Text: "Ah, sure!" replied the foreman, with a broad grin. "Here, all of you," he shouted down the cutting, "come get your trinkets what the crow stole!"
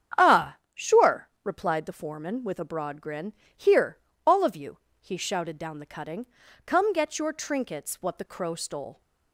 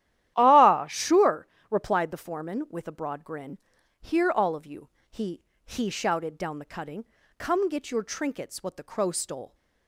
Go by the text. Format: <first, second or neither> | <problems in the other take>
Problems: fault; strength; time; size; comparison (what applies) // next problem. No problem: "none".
first | starts louder than the rest; strong; until 1.3 s; 12.5 dB; strong in the first // says "he" twice; at 5.6 s